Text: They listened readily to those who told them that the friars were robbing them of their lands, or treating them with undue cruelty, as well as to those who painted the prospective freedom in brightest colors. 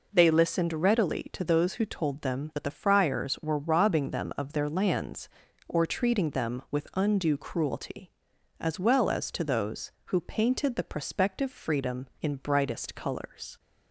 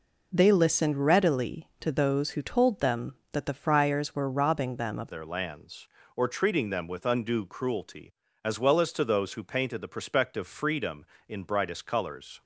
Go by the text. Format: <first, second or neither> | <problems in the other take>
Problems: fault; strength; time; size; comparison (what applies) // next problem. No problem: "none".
first | changes voice at "their"; from 5.1 s on; 7.3 s long